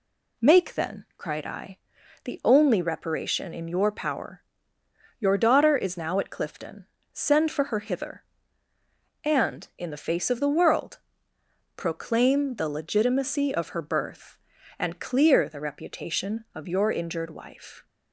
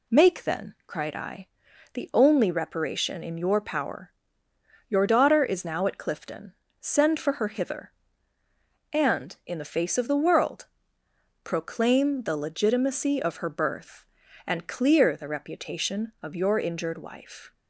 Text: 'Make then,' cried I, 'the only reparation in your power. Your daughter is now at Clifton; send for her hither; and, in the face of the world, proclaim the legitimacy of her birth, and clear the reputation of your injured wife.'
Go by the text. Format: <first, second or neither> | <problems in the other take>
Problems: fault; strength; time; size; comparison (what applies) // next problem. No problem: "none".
neither | none